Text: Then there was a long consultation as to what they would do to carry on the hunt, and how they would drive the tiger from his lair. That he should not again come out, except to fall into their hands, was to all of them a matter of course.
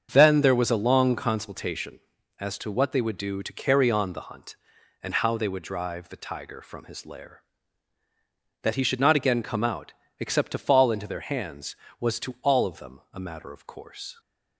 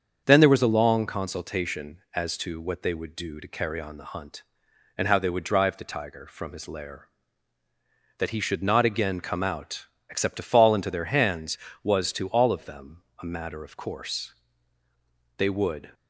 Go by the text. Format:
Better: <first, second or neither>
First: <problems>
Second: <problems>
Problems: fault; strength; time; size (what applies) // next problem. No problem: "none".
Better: first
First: starts louder than the rest; until 1.1 s; 7 dB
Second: starts louder than the rest; until 1.2 s; 7 dB // pauses between "them" and "a"; slight; at 13.0 s; 0.20 s long // goes on to say "They would"; from 15.3 s on; 0.56 s long